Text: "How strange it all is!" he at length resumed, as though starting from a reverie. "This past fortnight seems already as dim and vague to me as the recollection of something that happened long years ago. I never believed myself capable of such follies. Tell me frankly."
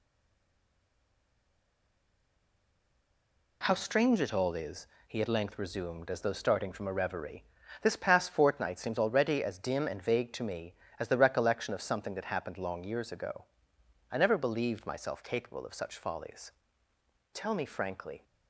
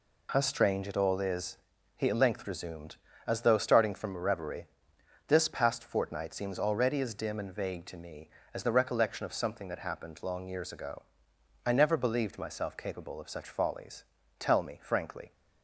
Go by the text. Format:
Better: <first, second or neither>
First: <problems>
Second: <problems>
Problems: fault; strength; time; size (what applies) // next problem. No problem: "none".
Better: second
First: stays silent before the first word; strong; until 3.6 s; 3.6 s long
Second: none